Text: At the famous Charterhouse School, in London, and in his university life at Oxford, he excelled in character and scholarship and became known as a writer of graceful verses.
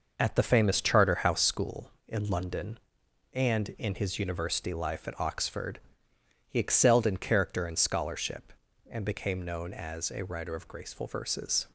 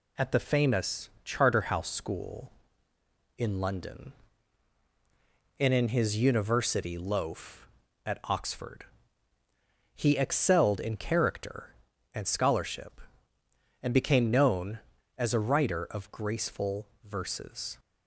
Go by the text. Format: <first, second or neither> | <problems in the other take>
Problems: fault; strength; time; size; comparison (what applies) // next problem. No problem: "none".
first | pauses between "famous" and "Charterhouse"; slight; at 1.0 s; 0.16 s long // says "loaf" for "life"; at 6.9 s // pauses between "graceful" and "verses"; slight; at 16.8 s; 0.18 s long